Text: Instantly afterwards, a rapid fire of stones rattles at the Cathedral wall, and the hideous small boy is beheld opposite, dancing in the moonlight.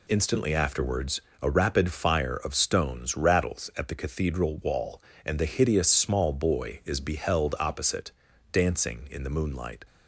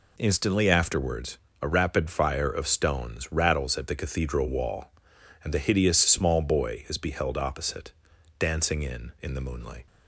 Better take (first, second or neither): first